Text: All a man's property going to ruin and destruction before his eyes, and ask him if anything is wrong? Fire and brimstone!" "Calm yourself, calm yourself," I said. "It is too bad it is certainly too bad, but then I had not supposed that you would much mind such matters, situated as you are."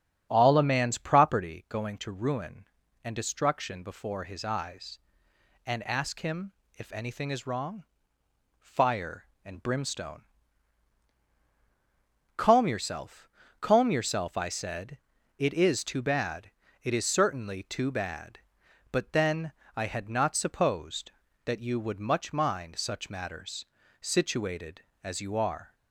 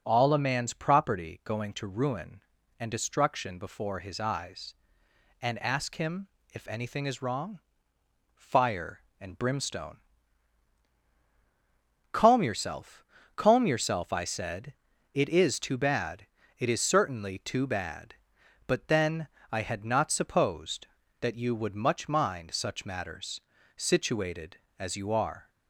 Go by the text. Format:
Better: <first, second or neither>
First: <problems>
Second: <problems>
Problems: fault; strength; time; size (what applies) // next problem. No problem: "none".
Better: second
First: starts louder than the rest; strong; until 1.5 s; 8 dB // pauses between "him" and "if"; slight; at 6.5 s; 0.26 s long // pauses between "bad" and "it"; slight; at 16.5 s; 0.32 s long // pauses between "then" and "I"; slight; at 19.5 s; 0.24 s long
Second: pauses between "him" and "if"; slight; at 6.2 s; 0.26 s long // pauses between "bad" and "it"; slight; at 16.2 s; 0.32 s long // pauses between "then" and "I"; slight; at 19.2 s; 0.24 s long